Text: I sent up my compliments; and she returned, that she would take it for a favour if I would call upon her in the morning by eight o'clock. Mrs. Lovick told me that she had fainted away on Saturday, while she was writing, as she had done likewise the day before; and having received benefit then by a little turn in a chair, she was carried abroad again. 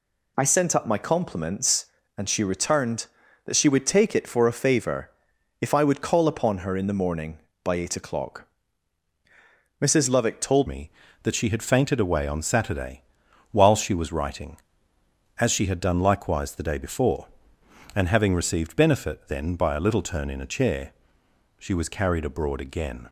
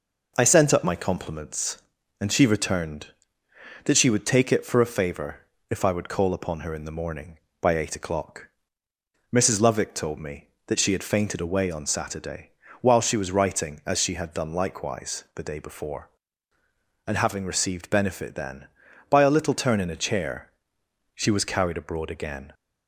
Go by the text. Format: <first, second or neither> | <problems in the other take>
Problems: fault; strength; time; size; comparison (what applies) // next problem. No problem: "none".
second | pauses between "favour" and "if"; noticeable; at 5.1 s; 0.50 s long; slight in the second // changes voice at "me"; from 10.6 s on; 12.4 s long